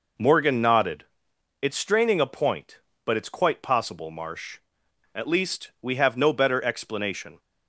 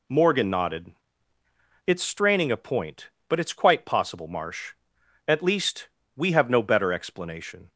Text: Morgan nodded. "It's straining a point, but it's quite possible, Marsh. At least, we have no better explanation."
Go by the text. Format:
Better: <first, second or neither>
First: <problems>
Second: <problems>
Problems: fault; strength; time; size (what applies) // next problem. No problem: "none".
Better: neither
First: none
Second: none